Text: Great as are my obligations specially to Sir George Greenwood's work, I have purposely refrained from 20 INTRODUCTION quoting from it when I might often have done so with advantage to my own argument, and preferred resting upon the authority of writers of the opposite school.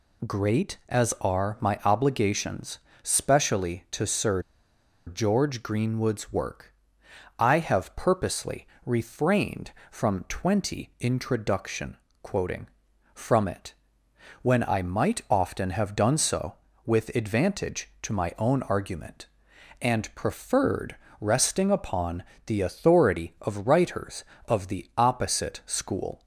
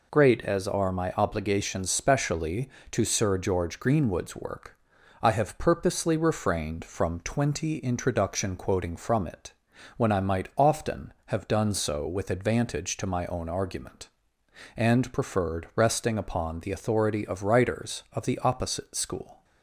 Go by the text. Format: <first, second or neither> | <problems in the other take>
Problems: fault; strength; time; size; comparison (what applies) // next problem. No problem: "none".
second | pauses between "obligations" and "specially"; slight; at 2.7 s; 0.24 s long // pauses between "Sir" and "George"; noticeable; at 4.4 s; 0.64 s long // pauses between "purposely" and "refrained"; slight; at 8.6 s; 0.18 s long // pauses between "INTRODUCTION" and "quoting"; slight; at 11.9 s; 0.26 s long // pauses between "it" and "when"; noticeable; at 13.7 s; 0.70 s long; noticeable in the second // pauses between "preferred" and "resting"; slight; at 20.9 s; 0.22 s long // pauses between "upon" and "the"; slight; at 22.2 s; 0.20 s long